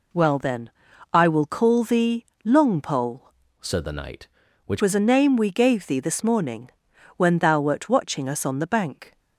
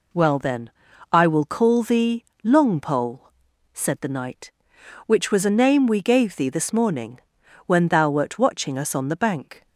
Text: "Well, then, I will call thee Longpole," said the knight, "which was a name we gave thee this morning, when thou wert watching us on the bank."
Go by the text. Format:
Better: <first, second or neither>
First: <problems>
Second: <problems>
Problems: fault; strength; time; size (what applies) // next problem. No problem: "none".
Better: second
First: pauses between "thee" and "Longpole"; slight; at 2.2 s; 0.20 s long // changes voice from "said" to "which"; from 3.6 to 4.8 s; 1.2 s long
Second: pauses between "thee" and "Longpole"; slight; at 2.2 s; 0.20 s long